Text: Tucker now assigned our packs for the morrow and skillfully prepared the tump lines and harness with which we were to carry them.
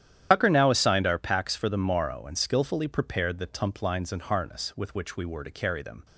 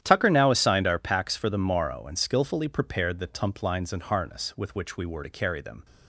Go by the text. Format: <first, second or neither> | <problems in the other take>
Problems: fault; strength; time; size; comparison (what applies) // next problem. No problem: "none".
second | loses the start of "Tucker"; at 0.3 s; 85 ms // starts louder than the rest; strong; until 1.3 s; 10.5 dB; strong in the second